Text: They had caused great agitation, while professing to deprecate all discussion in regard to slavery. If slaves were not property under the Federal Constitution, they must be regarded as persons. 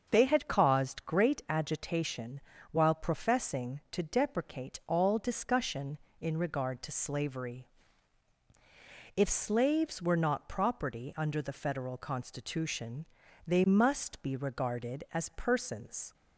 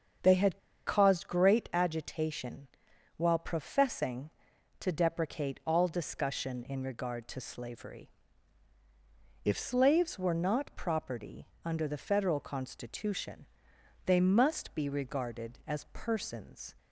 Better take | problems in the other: first | starts louder than the rest; until 1.5 s; 7 dB; also in the first // pauses between "had" and "caused"; slight; at 0.5 s; 0.28 s long // pauses between "property" and "under"; slight; at 11.4 s; 0.18 s long

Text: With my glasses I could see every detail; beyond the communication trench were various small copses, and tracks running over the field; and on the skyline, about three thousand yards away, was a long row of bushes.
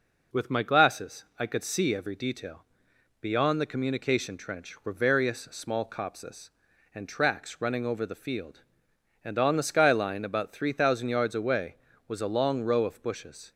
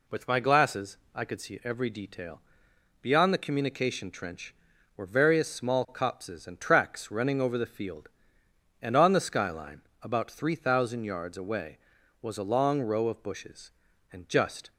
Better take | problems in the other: first | pauses between "glasses" and "I"; slight; at 0.9 s; 0.16 s long // goes on to say "And just"; from 14.1 s on; 0.60 s long

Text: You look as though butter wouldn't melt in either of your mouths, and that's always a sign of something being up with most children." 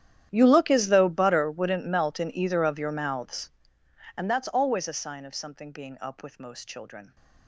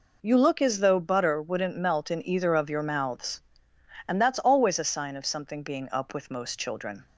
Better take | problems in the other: second | gets quieter; strong; throughout; 21.5 dB

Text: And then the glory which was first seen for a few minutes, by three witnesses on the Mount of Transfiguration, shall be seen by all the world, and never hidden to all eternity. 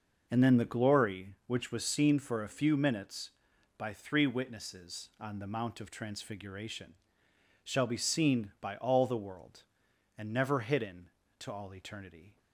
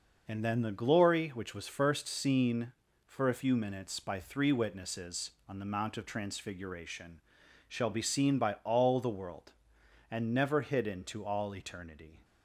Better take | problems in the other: second | skips "first"; at 1.8 s

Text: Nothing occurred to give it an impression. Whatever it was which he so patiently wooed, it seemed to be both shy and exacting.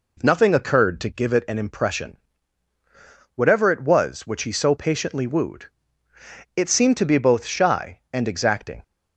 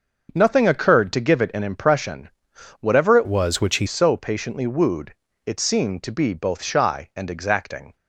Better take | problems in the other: first | starts louder than the rest; until 1.3 s; 6.5 dB // changes voice from "was" to "he"; from 3.2 to 3.8 s; 0.6 s long

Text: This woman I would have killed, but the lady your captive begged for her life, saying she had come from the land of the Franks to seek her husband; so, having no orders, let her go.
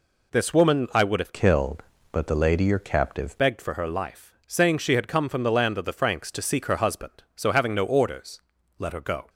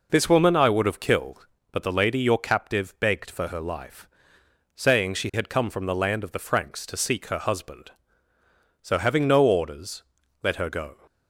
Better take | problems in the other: second | changes voice from "killed" to "captive"; from 1.3 to 3.3 s; 2.0 s long

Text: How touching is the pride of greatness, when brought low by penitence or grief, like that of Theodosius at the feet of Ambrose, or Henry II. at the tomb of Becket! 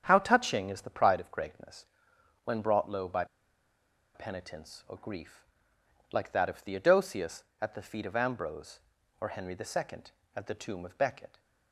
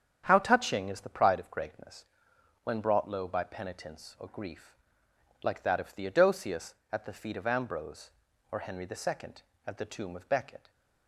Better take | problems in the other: second | starts louder than the rest; strong; until 1.0 s; 7.5 dB; strong in the second // pauses between "by" and "penitence"; noticeable; at 3.2 s; 0.89 s long

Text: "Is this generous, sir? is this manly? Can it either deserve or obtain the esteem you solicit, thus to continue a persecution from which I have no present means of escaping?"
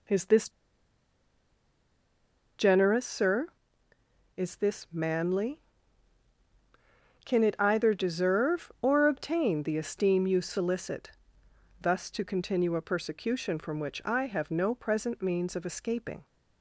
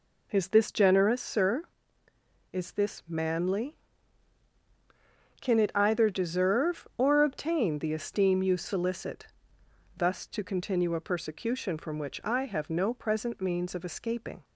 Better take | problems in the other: second | pauses between "this" and "generous"; strong; at 0.4 s; 2.0 s long

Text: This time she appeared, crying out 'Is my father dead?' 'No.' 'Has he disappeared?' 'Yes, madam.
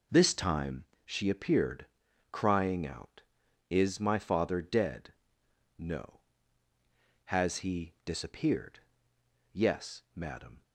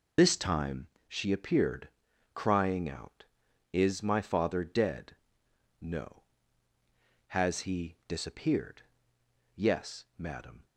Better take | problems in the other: first | loses the start of "This"; at 0.1 s; 50 ms // pauses between "time" and "she"; slight; at 0.8 s; 0.22 s long; slight in the first

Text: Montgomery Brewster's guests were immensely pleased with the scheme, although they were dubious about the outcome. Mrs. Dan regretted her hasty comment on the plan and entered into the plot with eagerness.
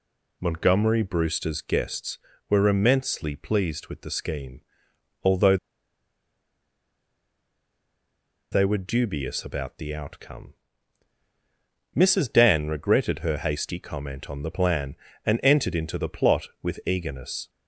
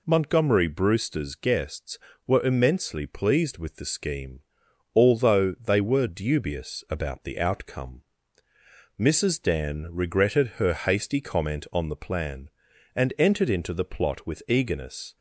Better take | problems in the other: second | pauses between "although" and "they"; strong; at 5.5 s; 2.9 s long

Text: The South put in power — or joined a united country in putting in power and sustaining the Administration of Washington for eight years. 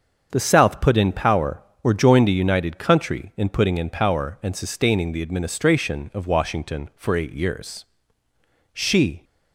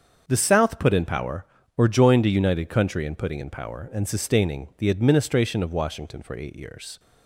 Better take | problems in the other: second | starts louder than the rest; until 1.3 s; 6.5 dB; also in the second // goes on to say "She"; from 8.7 s on; 0.52 s long

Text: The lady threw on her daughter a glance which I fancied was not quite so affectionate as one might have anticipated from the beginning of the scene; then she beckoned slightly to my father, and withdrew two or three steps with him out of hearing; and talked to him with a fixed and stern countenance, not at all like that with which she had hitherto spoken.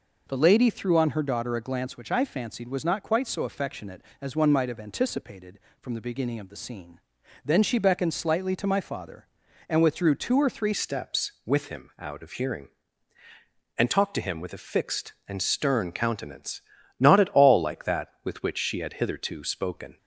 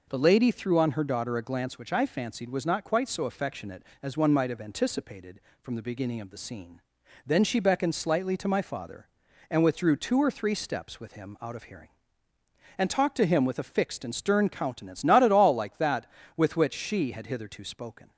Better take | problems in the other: second | changes voice at "steps"; from 10.7 s on; 9.2 s long

